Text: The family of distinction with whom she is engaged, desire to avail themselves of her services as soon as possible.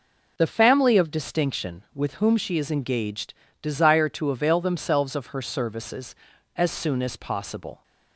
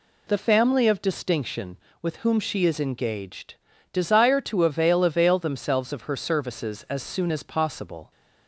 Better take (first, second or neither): first